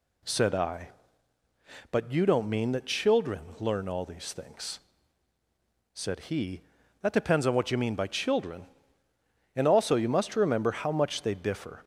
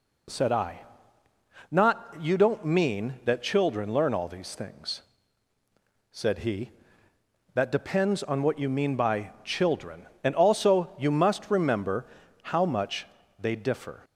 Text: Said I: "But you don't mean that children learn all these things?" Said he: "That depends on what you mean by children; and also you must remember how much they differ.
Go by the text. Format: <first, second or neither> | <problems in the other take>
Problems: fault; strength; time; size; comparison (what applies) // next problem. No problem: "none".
first | says "Not" for "But"; at 1.7 s // pauses between "remember" and "how"; at 12.0 s; 0.38 s long // pauses between "much" and "they"; slight; at 13.0 s; 0.32 s long